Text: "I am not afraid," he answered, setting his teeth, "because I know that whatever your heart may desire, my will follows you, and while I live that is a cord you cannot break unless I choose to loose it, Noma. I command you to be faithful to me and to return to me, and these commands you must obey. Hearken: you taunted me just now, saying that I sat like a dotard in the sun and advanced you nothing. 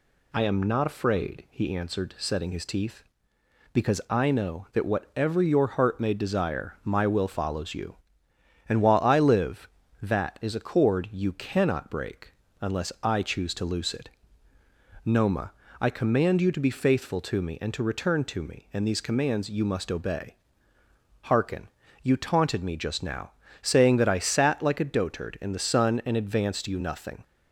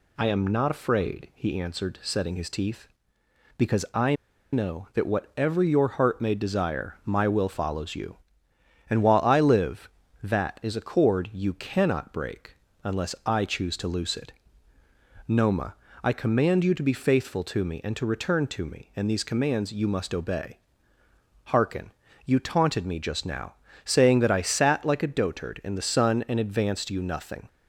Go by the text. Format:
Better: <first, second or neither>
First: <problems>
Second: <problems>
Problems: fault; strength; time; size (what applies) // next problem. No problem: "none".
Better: first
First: pauses between "break" and "unless"; slight; at 12.3 s; 0.30 s long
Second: pauses between "I" and "know"; at 4.1 s; 0.37 s long // pauses between "break" and "unless"; slight; at 12.5 s; 0.30 s long